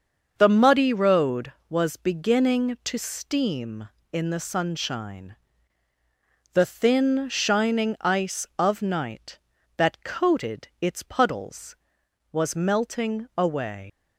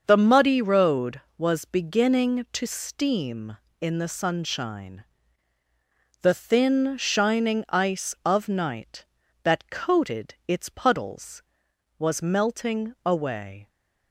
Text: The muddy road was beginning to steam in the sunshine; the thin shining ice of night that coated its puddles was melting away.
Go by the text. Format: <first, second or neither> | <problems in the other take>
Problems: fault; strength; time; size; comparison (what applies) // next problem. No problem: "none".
second | starts louder than the rest; until 1.3 s; 6.5 dB; also in the second // leaves "away" unfinished; at 13.8 s; 105 ms